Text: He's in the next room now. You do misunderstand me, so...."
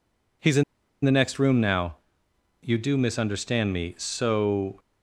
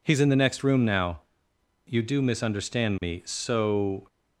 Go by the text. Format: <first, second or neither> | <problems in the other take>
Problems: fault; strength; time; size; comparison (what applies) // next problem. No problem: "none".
second | pauses between "in" and "the"; at 0.6 s; 0.39 s long